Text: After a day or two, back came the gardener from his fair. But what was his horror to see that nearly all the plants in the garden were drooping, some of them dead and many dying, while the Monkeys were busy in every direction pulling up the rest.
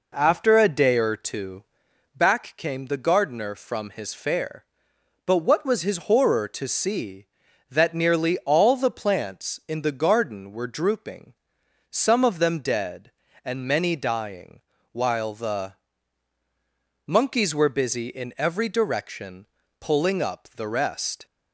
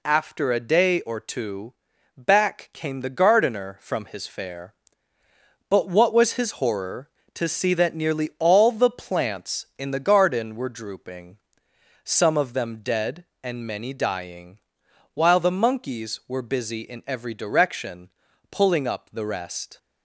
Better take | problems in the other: second | starts louder than the rest; noticeable; until 1.9 s; 4.5 dB // pauses between "the" and "Monkeys"; strong; at 15.7 s; 1.3 s long // pauses between "direction" and "pulling"; slight; at 19.4 s; 0.34 s long; also in the second

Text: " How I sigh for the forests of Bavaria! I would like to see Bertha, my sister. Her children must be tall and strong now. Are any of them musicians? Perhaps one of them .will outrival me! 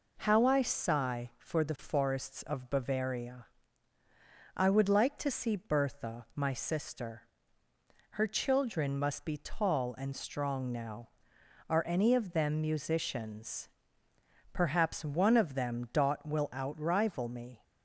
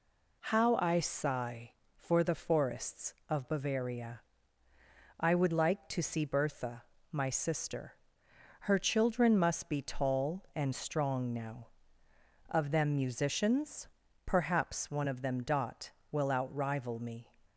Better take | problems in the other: first | skips "Are any"; at 12.0 s

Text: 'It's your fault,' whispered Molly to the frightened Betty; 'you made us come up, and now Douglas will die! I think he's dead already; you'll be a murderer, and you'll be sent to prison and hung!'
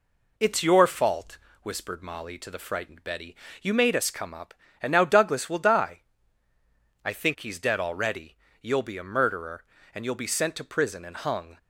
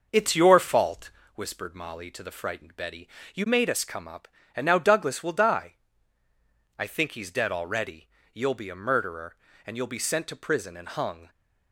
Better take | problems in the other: first | starts louder than the rest; noticeable; until 1.3 s; 6 dB

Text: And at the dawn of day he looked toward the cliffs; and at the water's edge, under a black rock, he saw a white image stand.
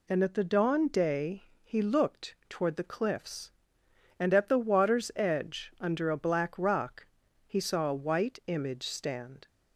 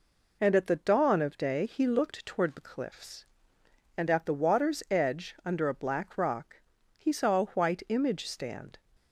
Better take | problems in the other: second | skips "of"; at 0.8 s // pauses between "day" and "he"; slight; at 1.4 s; 0.20 s long

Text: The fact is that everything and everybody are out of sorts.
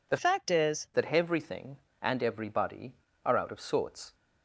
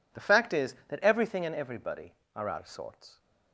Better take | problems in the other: second | changes voice from "fact" to "is"; from 0.1 to 0.8 s; 0.7 s long

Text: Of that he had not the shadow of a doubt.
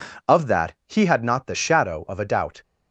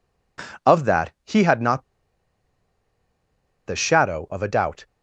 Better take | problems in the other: first | pauses between "not" and "the"; strong; at 1.8 s; 1.8 s long

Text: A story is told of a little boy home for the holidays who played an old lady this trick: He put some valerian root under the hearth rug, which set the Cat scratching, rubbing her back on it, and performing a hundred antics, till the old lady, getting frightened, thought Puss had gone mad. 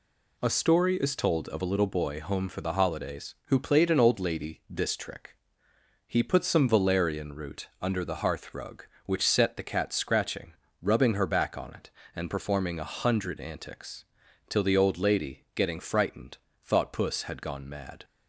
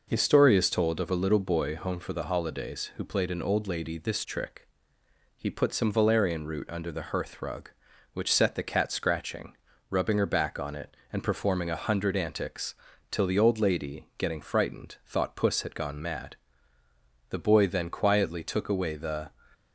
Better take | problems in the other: first | goes on to say "The boy then quietly took away the"; strong; from 17.2 s on; 2.0 s long

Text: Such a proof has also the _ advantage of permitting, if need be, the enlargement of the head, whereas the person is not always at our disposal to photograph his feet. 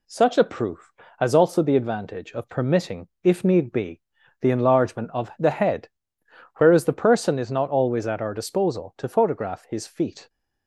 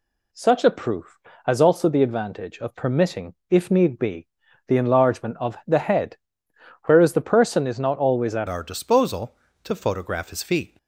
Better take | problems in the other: first | changes voice at "our"; from 8.4 s on; 2.3 s long

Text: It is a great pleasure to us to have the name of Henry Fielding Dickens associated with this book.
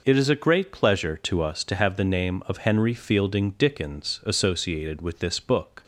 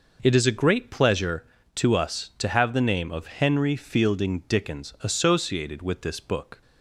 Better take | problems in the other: neither | none

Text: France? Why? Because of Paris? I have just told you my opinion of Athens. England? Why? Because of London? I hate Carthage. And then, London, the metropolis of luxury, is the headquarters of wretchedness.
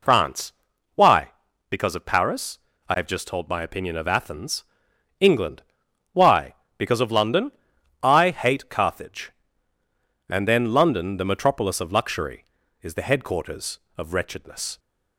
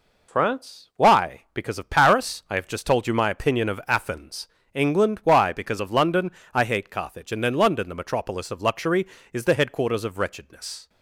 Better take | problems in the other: second | skips "you"; at 3.4 s

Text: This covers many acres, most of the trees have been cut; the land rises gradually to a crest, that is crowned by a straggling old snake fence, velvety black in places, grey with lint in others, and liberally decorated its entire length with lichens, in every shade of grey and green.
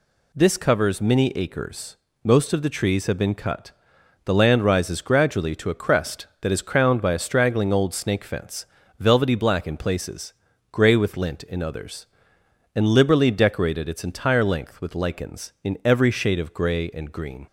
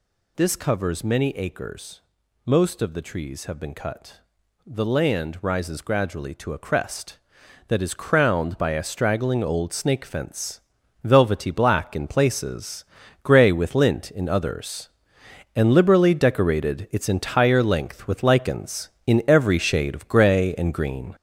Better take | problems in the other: first | gets louder; throughout; 6.5 dB

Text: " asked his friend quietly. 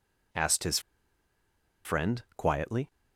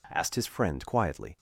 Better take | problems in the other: second | pauses between "his" and "friend"; at 0.7 s; 1.0 s long

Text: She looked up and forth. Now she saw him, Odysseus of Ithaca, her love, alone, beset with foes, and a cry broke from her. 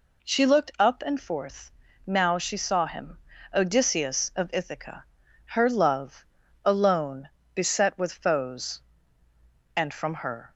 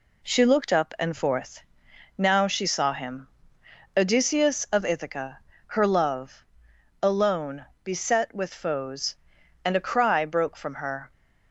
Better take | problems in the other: second | skips "a cry broke"; at 9.9 s

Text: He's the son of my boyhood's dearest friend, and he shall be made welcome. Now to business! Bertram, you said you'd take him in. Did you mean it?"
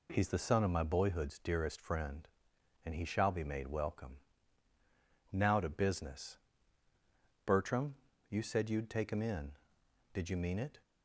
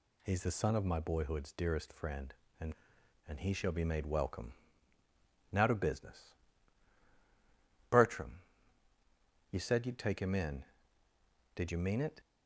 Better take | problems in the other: first | says "and" twice; at 3.2 s

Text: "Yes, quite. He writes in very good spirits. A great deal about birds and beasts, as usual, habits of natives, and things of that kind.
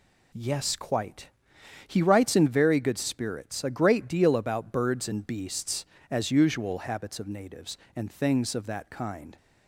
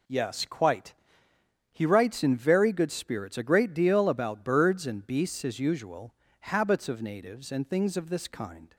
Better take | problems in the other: first | says "this" for "that"; at 8.0 s

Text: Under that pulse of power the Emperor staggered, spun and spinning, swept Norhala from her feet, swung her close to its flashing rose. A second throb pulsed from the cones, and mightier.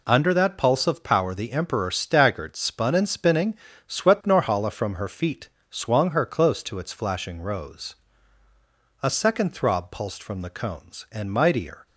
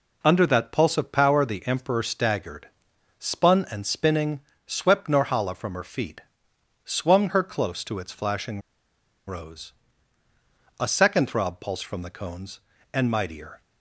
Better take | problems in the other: first | pauses between "flashing" and "rose"; noticeable; at 8.6 s; 0.66 s long

